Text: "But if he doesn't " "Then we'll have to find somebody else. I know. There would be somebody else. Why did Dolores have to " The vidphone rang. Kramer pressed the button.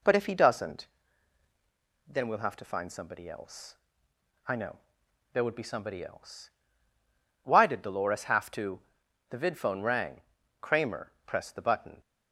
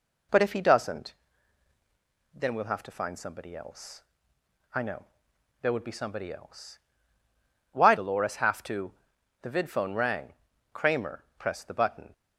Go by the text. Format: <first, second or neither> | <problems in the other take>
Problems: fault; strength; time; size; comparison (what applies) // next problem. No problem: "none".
first | skips "did"; at 7.9 s